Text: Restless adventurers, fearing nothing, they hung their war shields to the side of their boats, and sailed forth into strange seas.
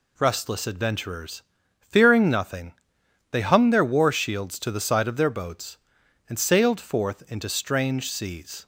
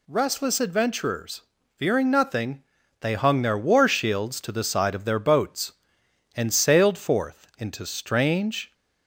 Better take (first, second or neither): first